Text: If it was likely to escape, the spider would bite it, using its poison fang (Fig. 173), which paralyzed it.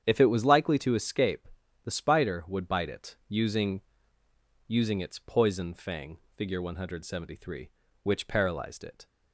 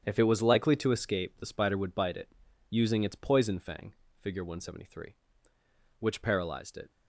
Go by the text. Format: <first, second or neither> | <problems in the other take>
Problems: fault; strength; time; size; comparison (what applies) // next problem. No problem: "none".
second | starts louder than the rest; strong; until 1.0 s; 8.5 dB; strong in the second // says "using" twice; at 4.6 s